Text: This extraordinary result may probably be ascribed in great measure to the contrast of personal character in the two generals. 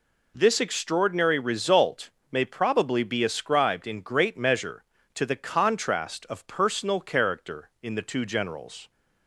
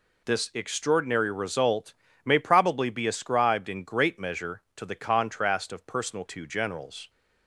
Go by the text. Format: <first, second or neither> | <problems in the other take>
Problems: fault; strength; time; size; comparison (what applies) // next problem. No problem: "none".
first | pauses between "result" and "may"; slight; at 1.9 s; 0.30 s long; slight in the first // skips "character in the"; at 6.2 s